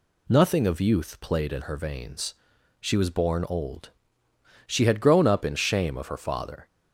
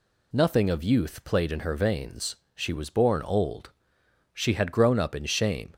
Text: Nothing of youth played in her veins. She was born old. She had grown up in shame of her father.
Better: first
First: none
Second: stops before "of her father"; at 5.7 s

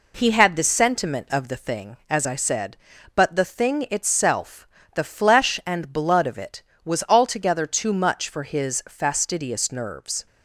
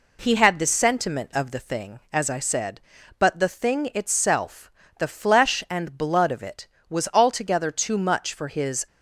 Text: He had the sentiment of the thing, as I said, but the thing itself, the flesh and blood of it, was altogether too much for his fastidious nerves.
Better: first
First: none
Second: stops before "fastidious nerves"; at 8.8 s

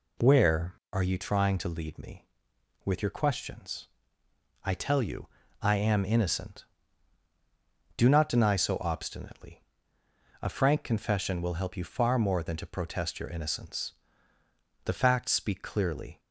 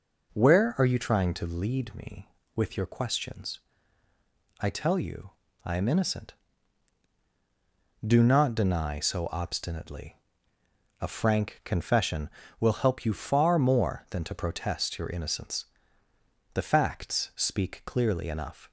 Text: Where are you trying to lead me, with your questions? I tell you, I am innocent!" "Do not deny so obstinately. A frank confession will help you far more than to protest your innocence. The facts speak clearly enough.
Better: second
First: stops before "enough"; at 16.1 s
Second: none

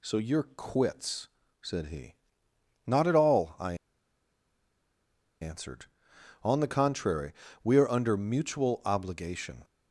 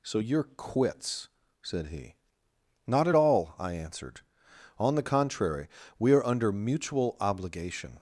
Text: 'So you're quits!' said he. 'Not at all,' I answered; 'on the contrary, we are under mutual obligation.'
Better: second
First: pauses between "I" and "answered"; strong; at 3.7 s; 1.6 s long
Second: none

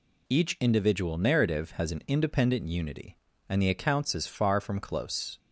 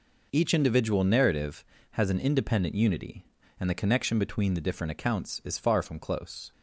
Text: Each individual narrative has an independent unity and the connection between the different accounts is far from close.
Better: second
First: skips "connection between the different"; at 3.6 s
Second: none

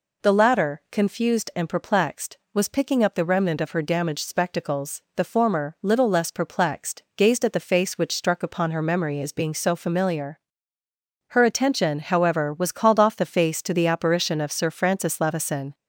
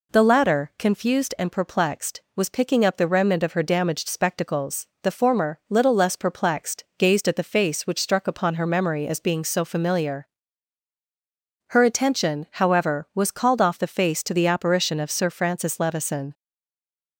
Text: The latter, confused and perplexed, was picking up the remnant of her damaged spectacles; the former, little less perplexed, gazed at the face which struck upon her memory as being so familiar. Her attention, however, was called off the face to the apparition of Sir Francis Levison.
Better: first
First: none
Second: stays silent after the last word; slight; from 16.3 s on; 0.8 s long

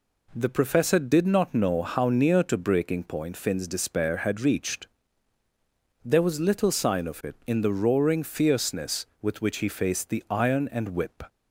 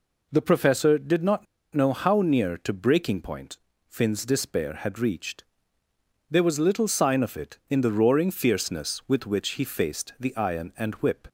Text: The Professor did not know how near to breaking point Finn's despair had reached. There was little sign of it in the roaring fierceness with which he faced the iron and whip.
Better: first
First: none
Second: pauses between "not" and "know"; slight; at 1.4 s; 0.29 s long // pauses between "point" and "Finn's"; slight; at 3.5 s; 0.32 s long

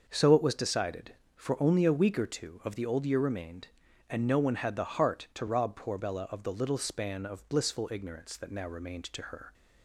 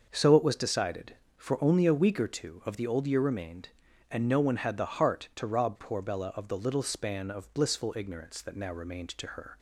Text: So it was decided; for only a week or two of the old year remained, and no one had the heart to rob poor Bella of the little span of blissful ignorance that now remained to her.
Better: neither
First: starts louder than the rest; until 1.0 s; 6 dB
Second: starts louder than the rest; until 1.1 s; 6 dB

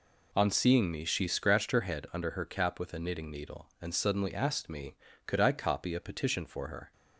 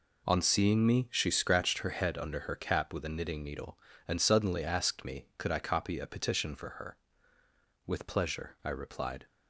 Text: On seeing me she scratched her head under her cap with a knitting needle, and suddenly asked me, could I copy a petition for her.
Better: first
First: none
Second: goes on to say "With pleasure I replied"; from 7.8 s on; 1.4 s long

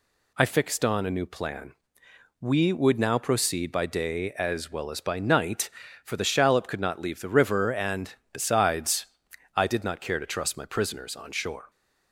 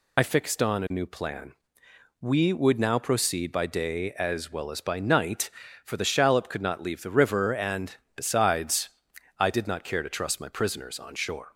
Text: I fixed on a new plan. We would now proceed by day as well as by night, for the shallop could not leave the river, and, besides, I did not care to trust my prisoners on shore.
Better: first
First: none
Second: loses the start of "I"; at 0.1 s; 50 ms

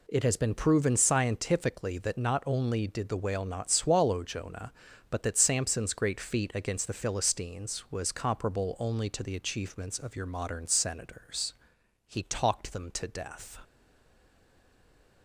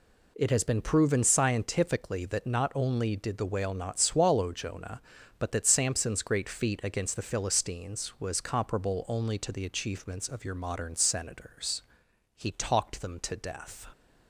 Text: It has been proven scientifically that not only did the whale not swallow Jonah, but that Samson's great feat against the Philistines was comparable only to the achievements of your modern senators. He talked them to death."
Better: second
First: stays silent after the last word; noticeable; from 13.6 s on; 1.6 s long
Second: none

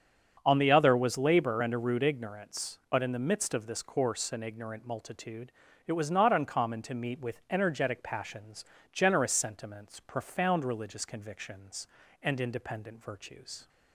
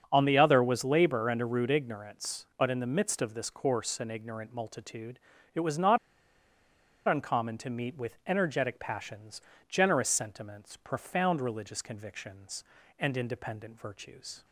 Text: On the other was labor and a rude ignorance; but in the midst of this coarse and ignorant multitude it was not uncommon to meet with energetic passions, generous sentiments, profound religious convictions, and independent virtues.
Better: first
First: starts louder than the rest; until 1.4 s; 7 dB // pauses between "multitude" and "it"; slight; at 5.5 s; 0.36 s long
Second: starts louder than the rest; until 1.1 s; 7 dB // pauses between "multitude" and "it"; slight; at 5.1 s; 0.36 s long // pauses between "not" and "uncommon"; at 5.9 s; 1.1 s long

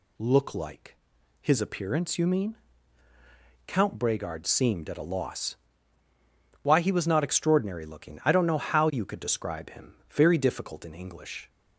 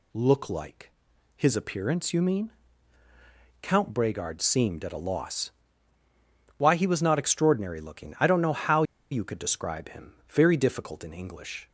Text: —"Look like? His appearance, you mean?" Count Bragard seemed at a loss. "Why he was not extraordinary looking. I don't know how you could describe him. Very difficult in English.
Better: first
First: none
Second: pauses between "how" and "you"; slight; at 8.8 s; 0.28 s long

